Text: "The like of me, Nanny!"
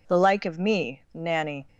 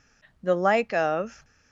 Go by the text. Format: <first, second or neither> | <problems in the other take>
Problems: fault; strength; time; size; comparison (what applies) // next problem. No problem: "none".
first | stops before "me Nanny"; at 1.4 s